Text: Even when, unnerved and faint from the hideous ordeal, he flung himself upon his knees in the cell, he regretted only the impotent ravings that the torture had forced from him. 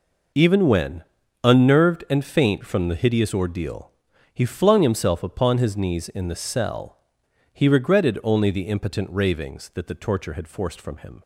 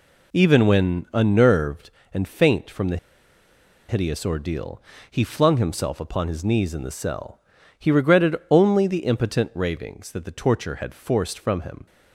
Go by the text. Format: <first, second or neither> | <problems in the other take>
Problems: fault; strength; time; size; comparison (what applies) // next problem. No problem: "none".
first | pauses between "the" and "hideous"; noticeable; at 2.9 s; 0.92 s long